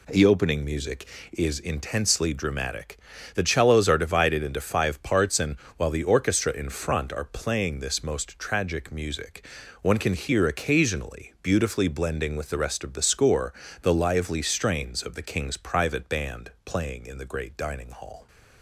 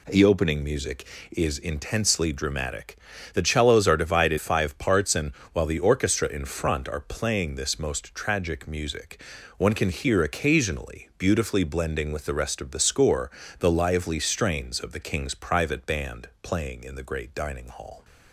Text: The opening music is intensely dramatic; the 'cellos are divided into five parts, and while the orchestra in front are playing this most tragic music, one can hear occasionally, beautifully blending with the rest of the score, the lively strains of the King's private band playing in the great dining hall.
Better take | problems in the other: first | skips "into"; at 4.3 s // pauses between "and" and "while"; slight; at 5.3 s; 0.22 s long; slight in the first // pauses between "band" and "playing"; slight; at 16.2 s; 0.16 s long; slight in the first

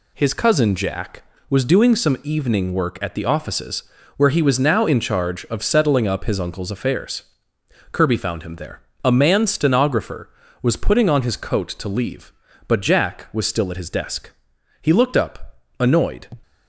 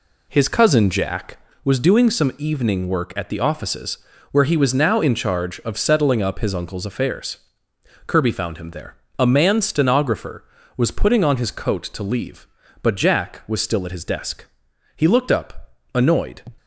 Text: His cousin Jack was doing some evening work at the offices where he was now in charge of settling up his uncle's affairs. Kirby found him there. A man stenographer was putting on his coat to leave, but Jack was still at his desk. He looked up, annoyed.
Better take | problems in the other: first | starts louder than the rest; slight; until 1.6 s; 2.5 dB // pauses between "offices" and "where"; slight; at 3.9 s; 0.32 s long; slight in the first

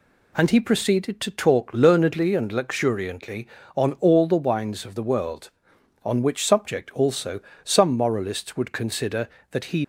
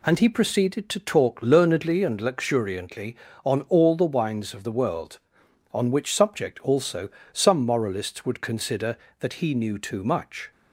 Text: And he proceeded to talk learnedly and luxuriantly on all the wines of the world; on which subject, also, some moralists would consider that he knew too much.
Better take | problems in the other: second | stops before "knew too much"; at 9.8 s

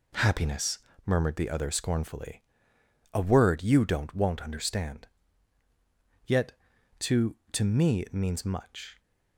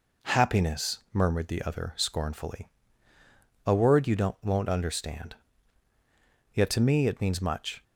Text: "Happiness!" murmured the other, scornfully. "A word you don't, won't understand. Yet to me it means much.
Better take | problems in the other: second | says "to" twice; at 7.5 s

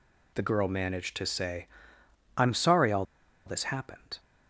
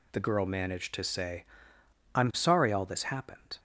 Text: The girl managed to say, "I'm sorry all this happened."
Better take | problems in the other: second | pauses between "all" and "this"; at 3.0 s; 0.41 s long

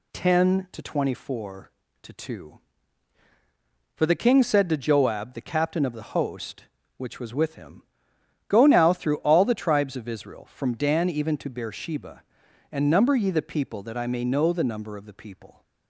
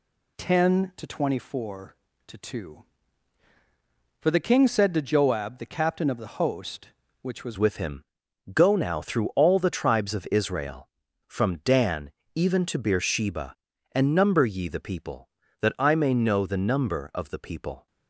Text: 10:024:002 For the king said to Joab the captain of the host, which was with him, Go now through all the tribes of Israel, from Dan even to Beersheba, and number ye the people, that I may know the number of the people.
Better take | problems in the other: first | changes voice at "with"; from 7.5 s on; 10.3 s long // pauses between "Dan" and "even"; slight; at 12.1 s; 0.24 s long

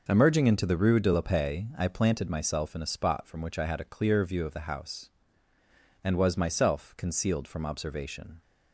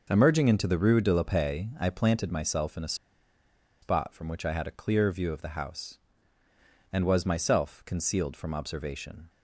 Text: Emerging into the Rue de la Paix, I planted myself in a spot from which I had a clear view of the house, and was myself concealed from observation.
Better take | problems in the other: first | pauses between "a" and "spot"; noticeable; at 2.9 s; 0.87 s long

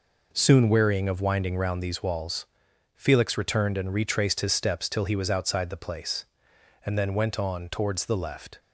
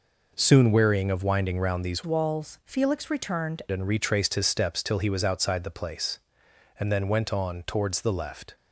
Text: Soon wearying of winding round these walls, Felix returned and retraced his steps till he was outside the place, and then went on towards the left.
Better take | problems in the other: first | changes voice from "walls" to "returned"; from 2.0 to 3.6 s; 1.6 s long

